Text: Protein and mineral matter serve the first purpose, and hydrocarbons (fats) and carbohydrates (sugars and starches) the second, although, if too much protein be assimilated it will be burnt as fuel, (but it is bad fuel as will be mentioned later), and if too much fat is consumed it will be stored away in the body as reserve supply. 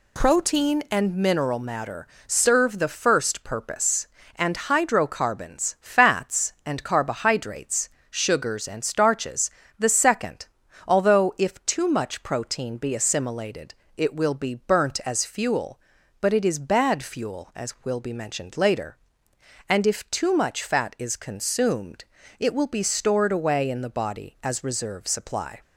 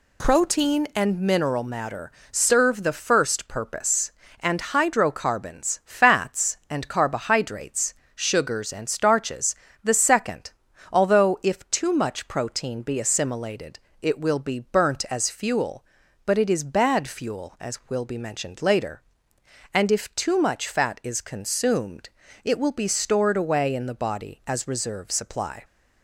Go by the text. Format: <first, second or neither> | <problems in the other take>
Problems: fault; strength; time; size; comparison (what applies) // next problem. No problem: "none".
neither | pauses between "matter" and "serve"; slight; the same in both // pauses between "assimilated" and "it"; slight; the same in both // pauses between "consumed" and "it"; slight; the same in both